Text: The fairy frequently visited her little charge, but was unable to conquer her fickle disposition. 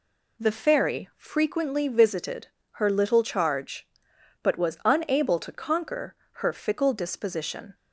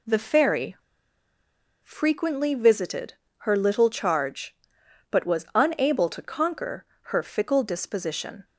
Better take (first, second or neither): first